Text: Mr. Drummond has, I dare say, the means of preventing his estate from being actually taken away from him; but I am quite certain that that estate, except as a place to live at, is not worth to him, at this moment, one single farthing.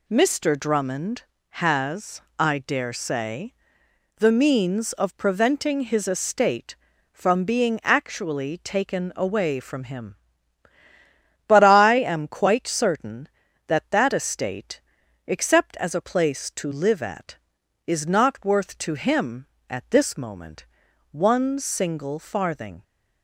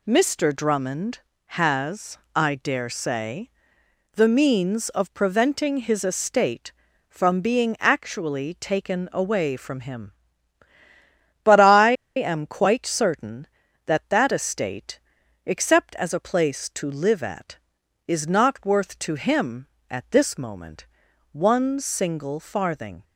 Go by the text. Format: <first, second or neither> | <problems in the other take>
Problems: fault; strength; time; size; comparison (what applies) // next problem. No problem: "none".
first | pauses between "I" and "am"; slight; at 11.9 s; 0.23 s long